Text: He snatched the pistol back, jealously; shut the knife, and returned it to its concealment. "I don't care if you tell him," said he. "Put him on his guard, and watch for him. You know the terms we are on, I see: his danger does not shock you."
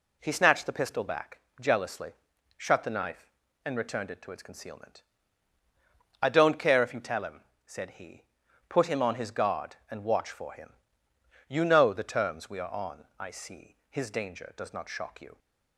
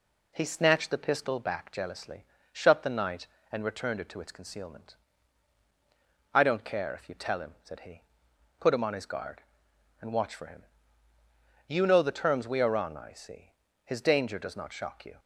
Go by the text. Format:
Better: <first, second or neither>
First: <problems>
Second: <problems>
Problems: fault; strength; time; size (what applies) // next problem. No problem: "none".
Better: first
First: none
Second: says "night" for "knife"; at 2.8 s